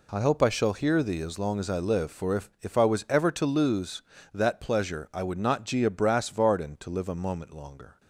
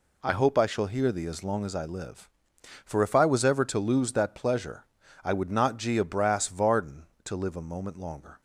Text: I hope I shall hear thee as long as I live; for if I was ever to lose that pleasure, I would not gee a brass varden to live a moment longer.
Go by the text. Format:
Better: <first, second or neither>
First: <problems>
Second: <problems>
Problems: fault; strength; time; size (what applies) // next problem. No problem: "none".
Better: second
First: says "if" twice; at 2.6 s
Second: none